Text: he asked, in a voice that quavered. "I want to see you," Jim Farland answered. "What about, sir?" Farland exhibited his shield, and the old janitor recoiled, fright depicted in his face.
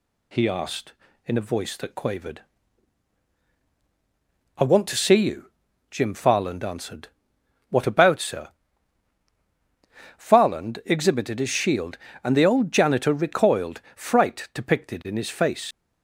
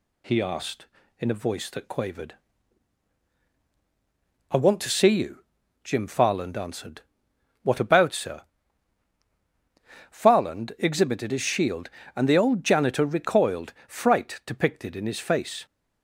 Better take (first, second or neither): second